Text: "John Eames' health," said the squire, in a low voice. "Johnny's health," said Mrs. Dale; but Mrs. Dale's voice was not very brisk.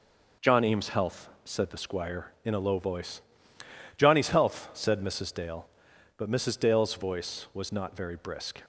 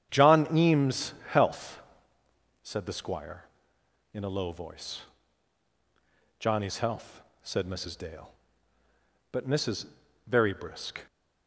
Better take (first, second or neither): first